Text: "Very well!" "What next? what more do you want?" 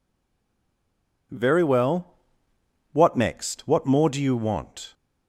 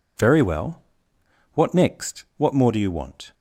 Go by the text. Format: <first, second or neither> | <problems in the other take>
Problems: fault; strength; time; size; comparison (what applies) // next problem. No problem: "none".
second | stays silent before the first word; noticeable; until 1.3 s; 1.3 s long